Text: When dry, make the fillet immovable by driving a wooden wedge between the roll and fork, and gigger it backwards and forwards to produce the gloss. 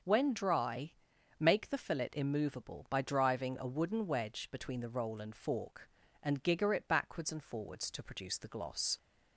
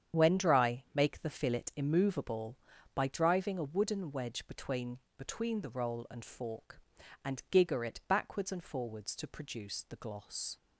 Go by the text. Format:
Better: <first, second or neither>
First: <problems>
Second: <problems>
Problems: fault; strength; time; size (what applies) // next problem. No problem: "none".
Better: first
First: starts louder than the rest; until 1.4 s; 6.5 dB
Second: starts louder than the rest; strong; until 1.2 s; 8.5 dB // says "between" twice; at 5.1 s